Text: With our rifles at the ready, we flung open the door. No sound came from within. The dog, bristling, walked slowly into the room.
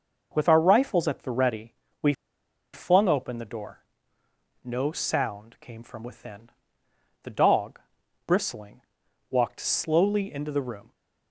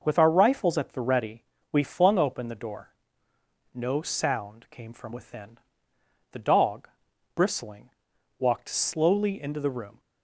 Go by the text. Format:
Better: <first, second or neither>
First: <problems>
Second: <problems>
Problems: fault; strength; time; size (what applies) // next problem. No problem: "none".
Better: second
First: pauses between "we" and "flung"; noticeable; at 2.1 s; 0.59 s long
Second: none